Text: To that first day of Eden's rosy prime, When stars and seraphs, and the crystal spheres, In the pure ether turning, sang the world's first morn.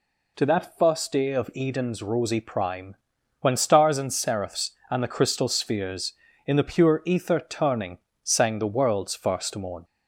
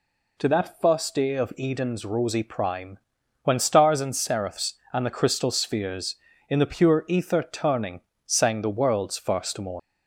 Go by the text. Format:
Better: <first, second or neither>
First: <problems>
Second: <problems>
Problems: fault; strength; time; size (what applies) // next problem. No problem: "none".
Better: first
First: none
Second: leaves "morn" unfinished; at 9.7 s; 75 ms